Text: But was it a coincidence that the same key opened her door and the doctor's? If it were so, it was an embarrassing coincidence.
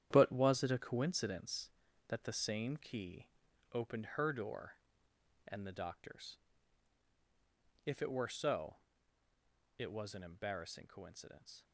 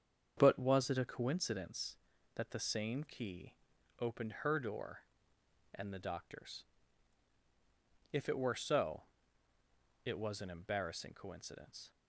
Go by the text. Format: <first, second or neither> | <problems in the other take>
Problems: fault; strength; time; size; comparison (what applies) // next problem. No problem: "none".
second | gets quieter; strong; throughout; 10 dB // starts louder than the rest; strong; until 1.1 s; 10 dB; strong in the second // pauses between "key" and "opened"; noticeable; at 3.2 s; 0.46 s long; noticeable in the second